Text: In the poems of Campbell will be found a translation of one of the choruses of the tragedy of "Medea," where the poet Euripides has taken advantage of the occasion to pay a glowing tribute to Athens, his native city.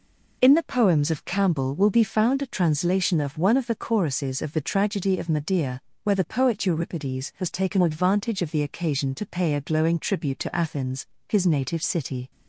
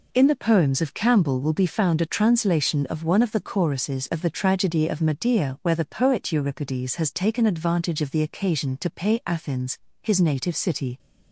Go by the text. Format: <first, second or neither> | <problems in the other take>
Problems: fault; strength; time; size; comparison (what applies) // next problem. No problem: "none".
first | skips "a glowing tribute to"; at 9.2 s